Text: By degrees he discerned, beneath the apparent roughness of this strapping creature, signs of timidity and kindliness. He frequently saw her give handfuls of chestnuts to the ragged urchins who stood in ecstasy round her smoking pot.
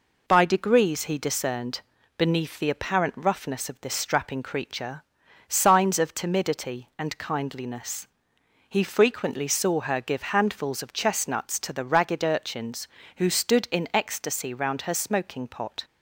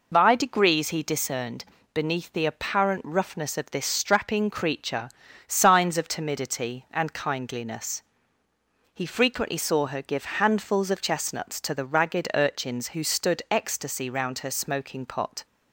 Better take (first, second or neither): first